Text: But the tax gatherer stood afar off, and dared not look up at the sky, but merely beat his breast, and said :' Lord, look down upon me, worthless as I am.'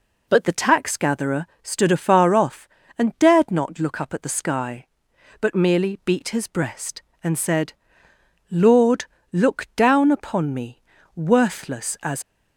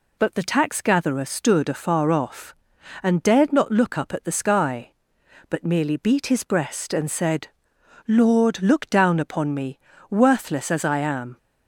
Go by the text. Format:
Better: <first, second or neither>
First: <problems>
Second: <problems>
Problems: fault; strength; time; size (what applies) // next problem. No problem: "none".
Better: second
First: pauses between "gatherer" and "stood"; slight; at 1.4 s; 0.16 s long // stops before "I am"; at 12.2 s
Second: none